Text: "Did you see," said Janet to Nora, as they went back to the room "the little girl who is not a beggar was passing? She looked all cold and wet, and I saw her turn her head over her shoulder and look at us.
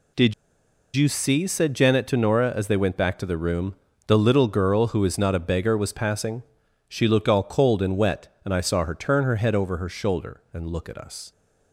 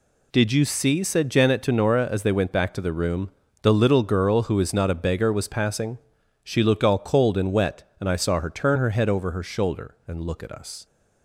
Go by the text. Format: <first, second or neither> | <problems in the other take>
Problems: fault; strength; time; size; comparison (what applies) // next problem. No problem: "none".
second | pauses between "Did" and "you"; noticeable; at 0.3 s; 0.62 s long // pauses between "room" and "the"; slight; at 3.7 s; 0.32 s long; slight in the second